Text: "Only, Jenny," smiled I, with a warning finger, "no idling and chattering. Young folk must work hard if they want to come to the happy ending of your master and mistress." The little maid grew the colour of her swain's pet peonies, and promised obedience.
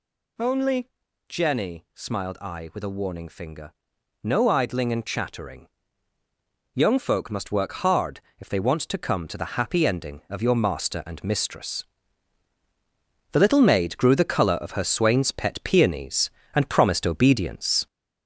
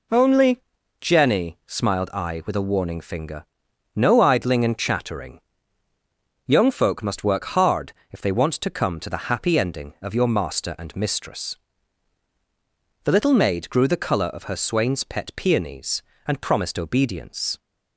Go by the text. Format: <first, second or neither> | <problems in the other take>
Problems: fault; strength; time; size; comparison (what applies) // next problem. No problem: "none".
second | gets louder; noticeable; throughout; 5 dB // pauses between "hard" and "if"; slight; at 8.2 s; 0.18 s long; slight in the second